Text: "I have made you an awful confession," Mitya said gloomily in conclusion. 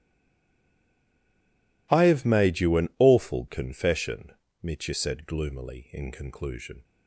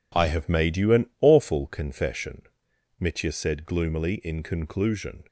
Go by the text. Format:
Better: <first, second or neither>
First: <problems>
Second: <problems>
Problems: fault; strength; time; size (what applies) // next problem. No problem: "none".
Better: second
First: stays silent before the first word; noticeable; until 1.9 s; 1.9 s long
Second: none